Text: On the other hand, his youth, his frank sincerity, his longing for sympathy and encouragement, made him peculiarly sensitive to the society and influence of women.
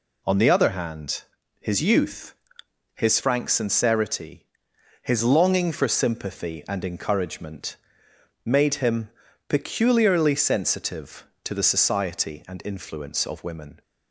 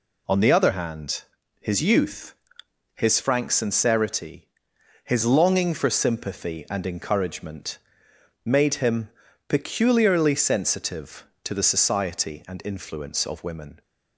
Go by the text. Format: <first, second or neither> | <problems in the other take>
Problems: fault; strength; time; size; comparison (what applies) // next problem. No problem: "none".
neither | pauses between "him" and "peculiarly"; the same in both